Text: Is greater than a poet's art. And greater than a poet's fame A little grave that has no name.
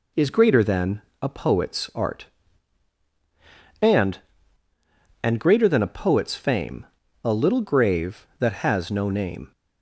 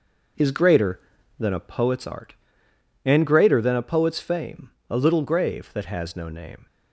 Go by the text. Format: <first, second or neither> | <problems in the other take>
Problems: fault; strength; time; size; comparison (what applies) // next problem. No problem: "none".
second | pauses between "than" and "a"; slight; at 1.0 s; 0.20 s long // says "And" twice; at 5.2 s // pauses between "fame" and "A"; at 6.8 s; 0.38 s long; slight in the second